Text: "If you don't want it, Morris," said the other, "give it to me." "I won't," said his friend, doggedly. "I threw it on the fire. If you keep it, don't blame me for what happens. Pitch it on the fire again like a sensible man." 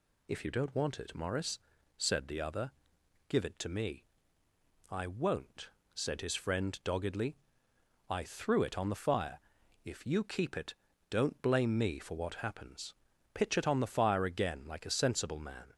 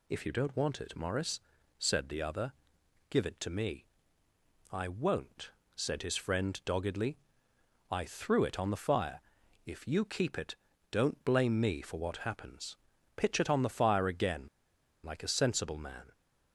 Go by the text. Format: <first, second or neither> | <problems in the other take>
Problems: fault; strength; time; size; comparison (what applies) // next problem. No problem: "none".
first | pauses between "again" and "like"; noticeable; at 14.4 s; 0.56 s long